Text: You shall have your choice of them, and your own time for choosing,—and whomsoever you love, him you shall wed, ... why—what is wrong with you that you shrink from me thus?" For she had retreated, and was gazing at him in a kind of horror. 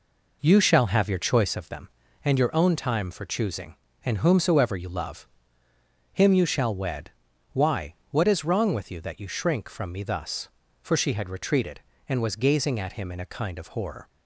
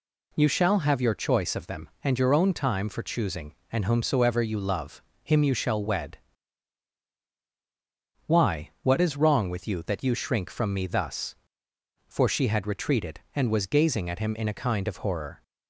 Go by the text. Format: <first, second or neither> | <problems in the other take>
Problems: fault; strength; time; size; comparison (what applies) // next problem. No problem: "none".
second | starts louder than the rest; noticeable; until 1.7 s; 4.5 dB